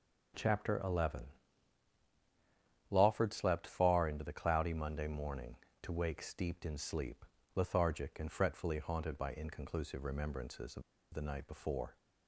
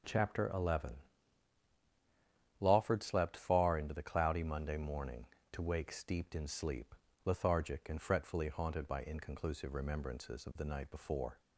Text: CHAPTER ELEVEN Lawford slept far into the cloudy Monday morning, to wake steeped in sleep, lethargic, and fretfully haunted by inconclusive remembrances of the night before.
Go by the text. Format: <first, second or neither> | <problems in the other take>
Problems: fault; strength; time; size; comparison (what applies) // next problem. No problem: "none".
second | starts louder than the rest; strong; until 3.0 s; 8 dB; strong in the second // pauses between "ELEVEN" and "Lawford"; strong; at 1.2 s; 1.7 s long; strong in the second // pauses between "of" and "the"; slight; at 10.8 s; 0.30 s long